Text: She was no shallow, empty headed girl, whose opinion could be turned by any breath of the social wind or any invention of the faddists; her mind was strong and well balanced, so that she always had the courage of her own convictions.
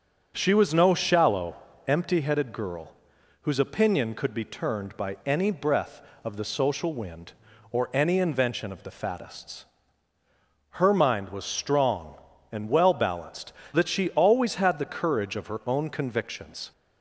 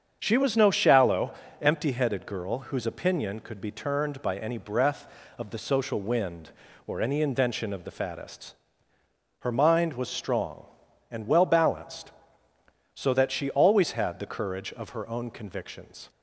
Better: second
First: starts louder than the rest; until 1.3 s; 6.5 dB // skips "so"; at 13.6 s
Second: starts louder than the rest; strong; until 1.2 s; 7.5 dB

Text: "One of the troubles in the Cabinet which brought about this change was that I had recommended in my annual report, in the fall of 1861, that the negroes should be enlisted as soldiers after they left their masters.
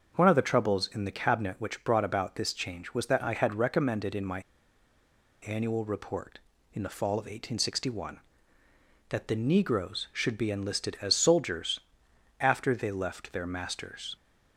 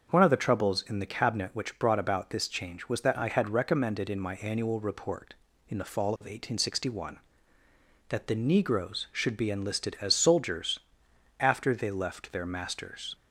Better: second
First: starts louder than the rest; until 1.2 s; 6.5 dB // pauses between "my" and "annual"; at 4.4 s; 1.0 s long // pauses between "soldiers" and "after"; noticeable; at 11.7 s; 0.60 s long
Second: starts louder than the rest; until 1.1 s; 6.5 dB // pauses between "soldiers" and "after"; noticeable; at 10.7 s; 0.60 s long

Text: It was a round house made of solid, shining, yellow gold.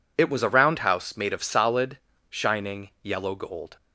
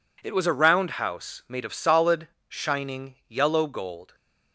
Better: neither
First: none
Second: none

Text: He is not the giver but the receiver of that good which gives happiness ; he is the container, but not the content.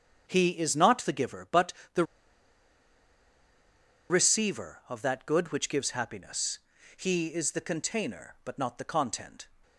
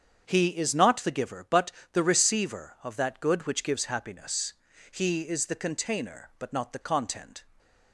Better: second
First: starts louder than the rest; strong; until 1.3 s; 7.5 dB // pauses between "but" and "the"; slight; at 1.7 s; 0.22 s long // pauses between "the" and "receiver"; strong; at 2.0 s; 2.0 s long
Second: starts louder than the rest; strong; until 1.2 s; 7.5 dB // pauses between "but" and "the"; slight; at 1.7 s; 0.22 s long

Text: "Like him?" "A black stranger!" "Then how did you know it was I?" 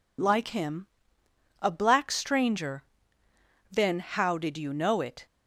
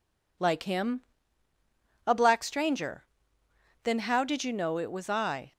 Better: second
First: stops before "was I"; at 5.2 s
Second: none

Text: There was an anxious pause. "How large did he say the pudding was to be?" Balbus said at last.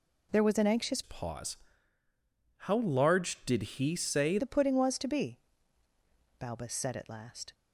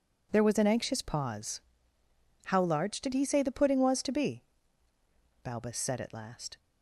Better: second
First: changes voice from "pause" to "say"; from 1.0 to 4.3 s; 3.3 s long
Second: none

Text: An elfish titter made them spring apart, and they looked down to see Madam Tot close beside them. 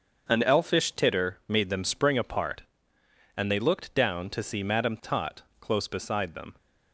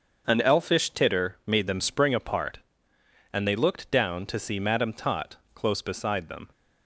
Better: neither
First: starts louder than the rest; until 1.3 s; 6.5 dB // pauses between "Tot" and "close"; slight; at 5.4 s; 0.18 s long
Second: starts louder than the rest; until 1.2 s; 6.5 dB // pauses between "Tot" and "close"; slight; at 5.3 s; 0.18 s long

